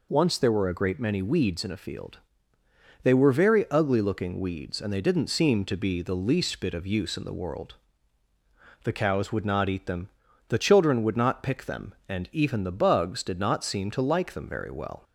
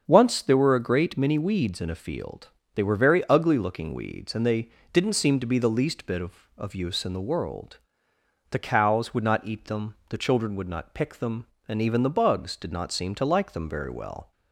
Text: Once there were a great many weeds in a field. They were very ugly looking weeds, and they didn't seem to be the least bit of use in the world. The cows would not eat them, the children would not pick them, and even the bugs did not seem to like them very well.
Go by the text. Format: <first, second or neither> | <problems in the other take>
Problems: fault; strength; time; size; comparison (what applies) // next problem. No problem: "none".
first | starts louder than the rest; until 1.0 s; 7 dB // pauses between "they" and "didn't"; slight; at 4.6 s; 0.24 s long // says "of" twice; at 6.5 s